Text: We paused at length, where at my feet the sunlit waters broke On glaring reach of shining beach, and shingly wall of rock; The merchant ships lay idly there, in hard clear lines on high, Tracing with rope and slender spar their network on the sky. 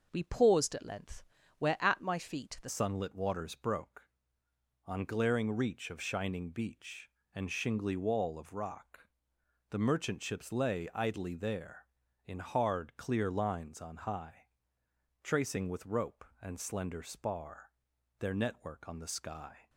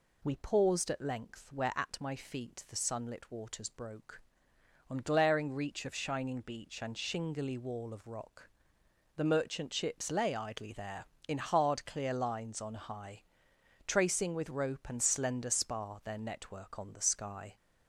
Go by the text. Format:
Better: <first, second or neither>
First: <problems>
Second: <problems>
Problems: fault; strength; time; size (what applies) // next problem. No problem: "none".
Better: second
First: starts louder than the rest; noticeable; until 1.1 s; 6 dB // changes voice at "sunlit"; from 2.6 s on; 17.0 s long // pauses between "spar" and "their"; noticeable; at 17.7 s; 0.48 s long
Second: none